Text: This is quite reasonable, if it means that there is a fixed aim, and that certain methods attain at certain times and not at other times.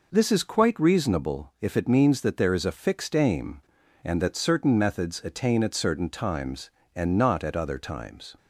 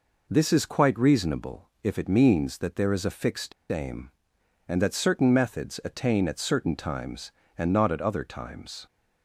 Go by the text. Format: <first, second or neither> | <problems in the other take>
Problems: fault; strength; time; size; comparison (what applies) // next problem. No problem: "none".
first | pauses between "fixed" and "aim"; slight; at 3.5 s; 0.18 s long